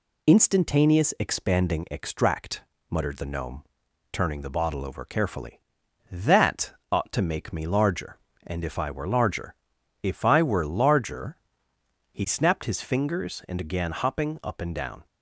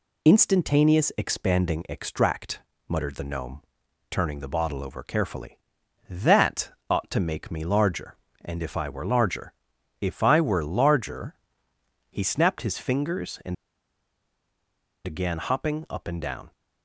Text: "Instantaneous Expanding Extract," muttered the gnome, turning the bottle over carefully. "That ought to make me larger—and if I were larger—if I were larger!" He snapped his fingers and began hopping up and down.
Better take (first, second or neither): first